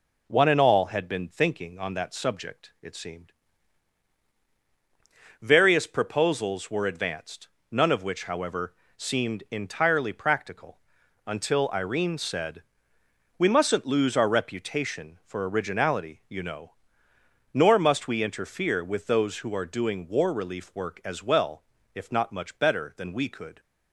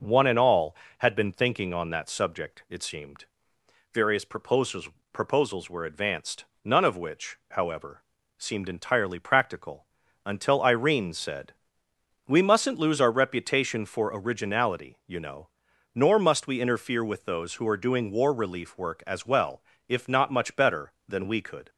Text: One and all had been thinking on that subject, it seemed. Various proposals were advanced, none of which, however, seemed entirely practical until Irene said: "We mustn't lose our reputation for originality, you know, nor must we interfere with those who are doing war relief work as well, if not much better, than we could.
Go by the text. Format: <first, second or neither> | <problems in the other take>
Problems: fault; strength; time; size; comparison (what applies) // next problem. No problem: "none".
first | says "proposals" twice; at 5.1 s // pauses between "practical" and "until"; at 9.8 s; 0.40 s long; noticeable in the first